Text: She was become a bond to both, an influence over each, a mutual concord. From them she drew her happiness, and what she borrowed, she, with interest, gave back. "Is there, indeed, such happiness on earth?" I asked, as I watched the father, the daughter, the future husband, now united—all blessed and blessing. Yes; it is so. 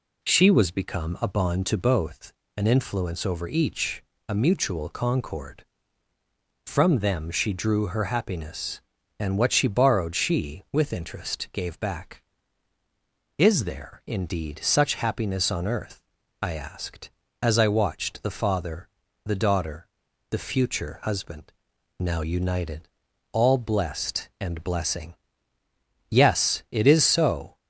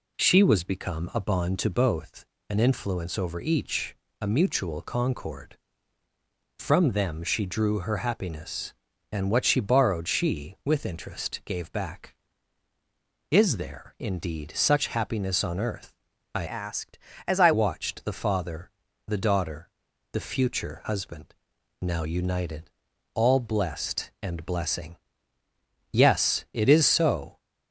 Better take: first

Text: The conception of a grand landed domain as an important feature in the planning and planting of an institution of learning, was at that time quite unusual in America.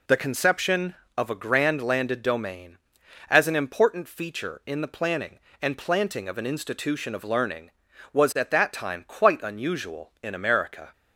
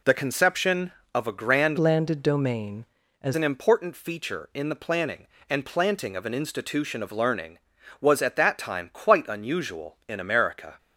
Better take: first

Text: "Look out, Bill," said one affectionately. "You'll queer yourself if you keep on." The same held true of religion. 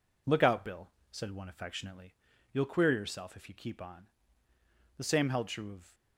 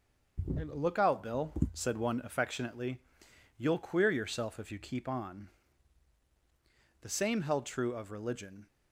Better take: second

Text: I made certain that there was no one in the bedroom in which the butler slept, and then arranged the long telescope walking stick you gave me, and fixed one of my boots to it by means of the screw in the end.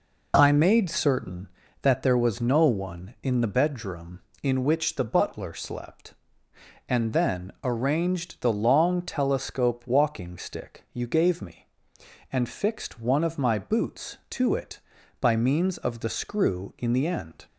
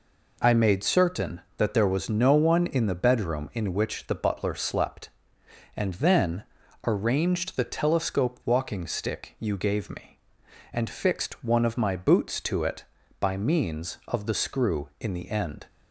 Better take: first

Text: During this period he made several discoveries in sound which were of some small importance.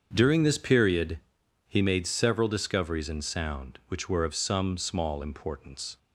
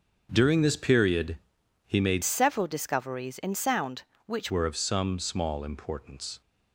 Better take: first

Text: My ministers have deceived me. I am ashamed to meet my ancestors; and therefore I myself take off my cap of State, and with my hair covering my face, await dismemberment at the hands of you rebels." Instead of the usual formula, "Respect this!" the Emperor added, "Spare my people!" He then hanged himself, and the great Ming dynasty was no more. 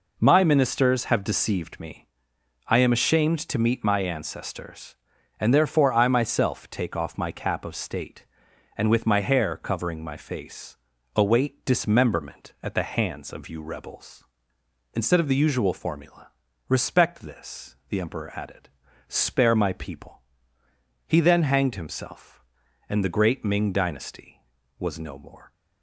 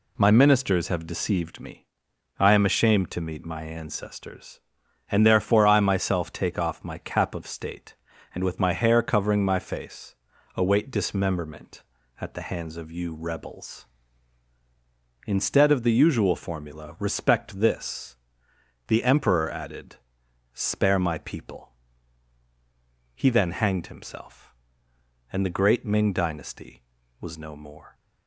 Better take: neither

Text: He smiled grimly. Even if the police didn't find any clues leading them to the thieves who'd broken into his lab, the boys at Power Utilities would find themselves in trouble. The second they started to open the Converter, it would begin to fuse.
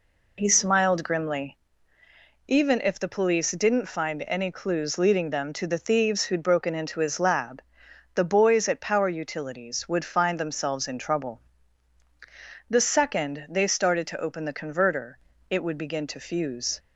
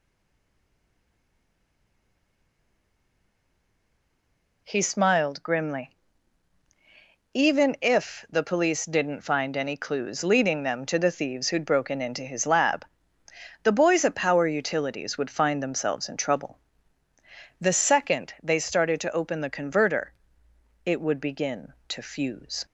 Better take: first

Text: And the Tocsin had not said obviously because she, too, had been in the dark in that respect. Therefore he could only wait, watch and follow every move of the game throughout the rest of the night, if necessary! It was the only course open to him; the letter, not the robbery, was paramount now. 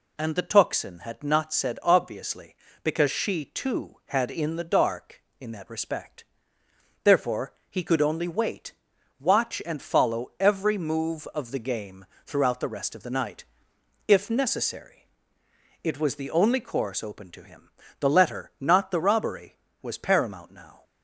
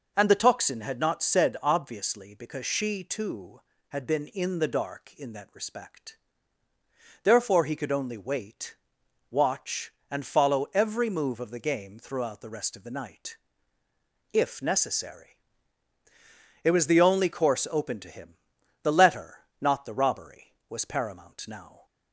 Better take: second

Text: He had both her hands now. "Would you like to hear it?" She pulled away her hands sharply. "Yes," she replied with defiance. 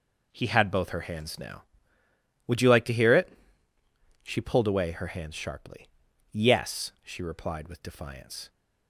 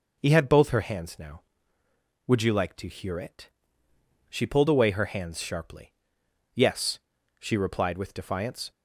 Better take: neither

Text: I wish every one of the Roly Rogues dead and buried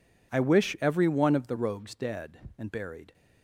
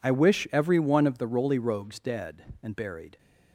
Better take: second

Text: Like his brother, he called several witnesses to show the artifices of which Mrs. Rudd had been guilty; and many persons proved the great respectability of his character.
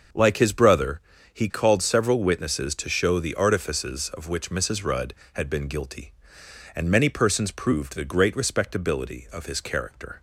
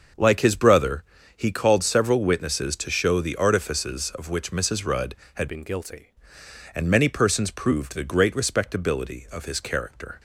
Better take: first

